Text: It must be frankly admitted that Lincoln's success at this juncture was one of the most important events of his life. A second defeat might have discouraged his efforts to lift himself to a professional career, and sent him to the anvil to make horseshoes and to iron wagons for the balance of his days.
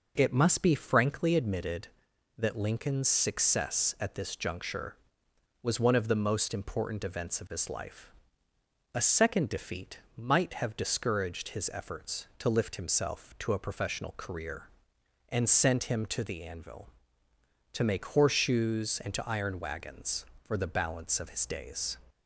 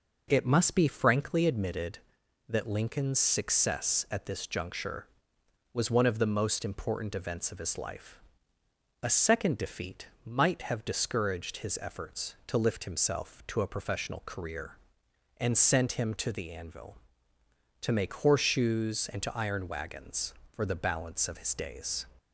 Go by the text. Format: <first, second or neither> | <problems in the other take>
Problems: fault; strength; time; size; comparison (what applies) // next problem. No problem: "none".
neither | pauses between "defeat" and "might"; slight; the same in both